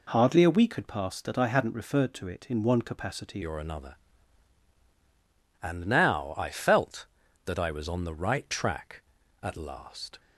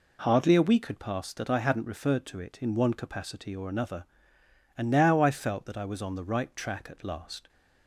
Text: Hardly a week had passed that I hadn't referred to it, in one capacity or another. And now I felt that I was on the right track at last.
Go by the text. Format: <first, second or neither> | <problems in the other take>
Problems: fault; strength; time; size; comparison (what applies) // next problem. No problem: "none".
second | changes voice at "or"; from 3.4 s on; 6.7 s long